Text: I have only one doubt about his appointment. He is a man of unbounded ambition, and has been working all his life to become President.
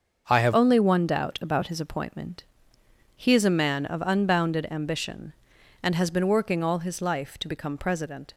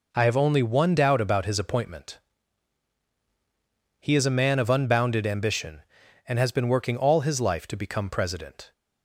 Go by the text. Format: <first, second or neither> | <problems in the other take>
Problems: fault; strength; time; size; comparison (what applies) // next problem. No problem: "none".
second | starts louder than the rest; until 1.2 s; 6.5 dB // changes voice at "only"; from 0.5 s on; 7.8 s long